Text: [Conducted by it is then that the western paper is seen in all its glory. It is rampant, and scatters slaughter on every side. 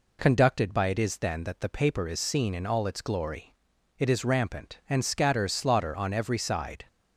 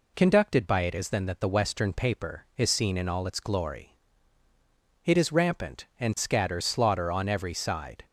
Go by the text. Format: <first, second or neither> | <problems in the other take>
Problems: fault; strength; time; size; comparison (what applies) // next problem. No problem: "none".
second | skips "western"; at 1.6 s